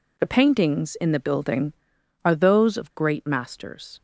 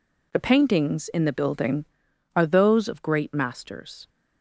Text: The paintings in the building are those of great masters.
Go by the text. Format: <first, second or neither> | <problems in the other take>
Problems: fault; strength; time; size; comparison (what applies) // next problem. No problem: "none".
neither | none